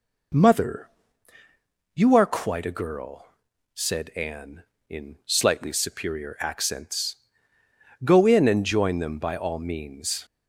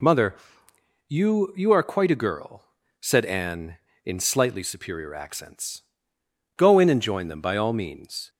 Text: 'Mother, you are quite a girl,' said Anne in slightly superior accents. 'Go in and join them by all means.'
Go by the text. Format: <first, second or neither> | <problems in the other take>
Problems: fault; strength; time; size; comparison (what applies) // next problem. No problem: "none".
first | says "you" twice; at 1.5 s